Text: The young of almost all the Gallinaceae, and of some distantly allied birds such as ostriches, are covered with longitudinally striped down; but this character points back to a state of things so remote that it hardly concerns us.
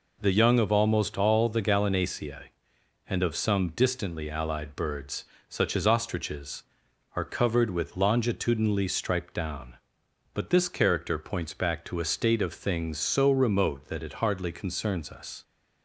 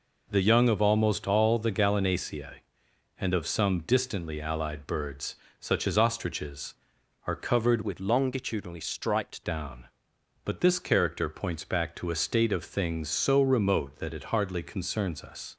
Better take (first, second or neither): first